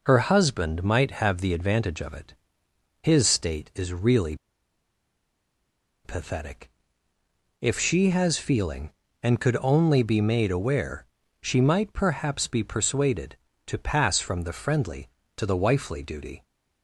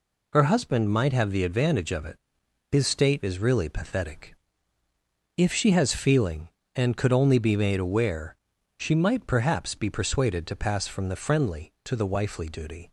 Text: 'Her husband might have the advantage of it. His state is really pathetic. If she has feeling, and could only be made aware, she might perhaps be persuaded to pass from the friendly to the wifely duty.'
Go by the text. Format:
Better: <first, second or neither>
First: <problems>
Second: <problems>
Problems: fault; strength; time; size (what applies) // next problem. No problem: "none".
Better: second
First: pauses between "really" and "pathetic"; strong; at 4.3 s; 1.6 s long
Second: none